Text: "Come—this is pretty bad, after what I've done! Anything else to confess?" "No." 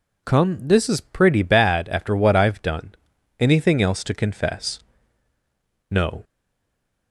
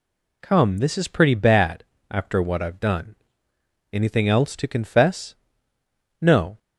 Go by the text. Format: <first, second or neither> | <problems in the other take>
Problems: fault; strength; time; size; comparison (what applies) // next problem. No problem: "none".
second | stays silent after the last word; slight; from 6.2 s on; 0.9 s long